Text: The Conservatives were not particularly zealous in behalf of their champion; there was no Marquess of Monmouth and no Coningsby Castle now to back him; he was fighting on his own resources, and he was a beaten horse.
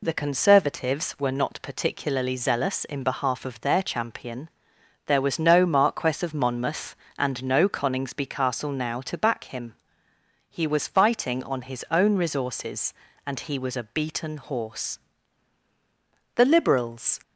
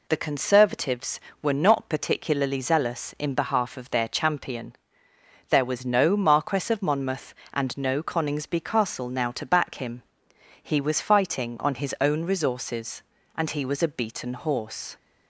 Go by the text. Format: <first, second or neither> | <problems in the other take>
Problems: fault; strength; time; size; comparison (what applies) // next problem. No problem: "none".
second | goes on to say "The Liberals"; noticeable; from 16.3 s on; 0.86 s long